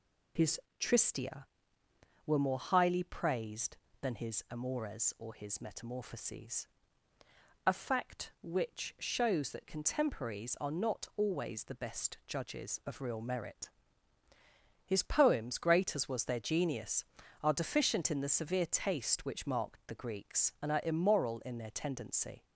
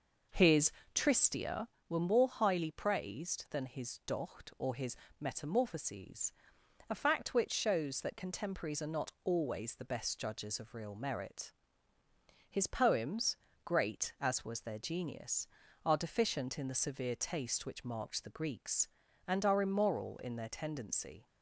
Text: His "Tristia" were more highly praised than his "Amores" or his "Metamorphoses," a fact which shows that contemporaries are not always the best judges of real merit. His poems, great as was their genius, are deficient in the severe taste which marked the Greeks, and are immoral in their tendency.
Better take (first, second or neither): first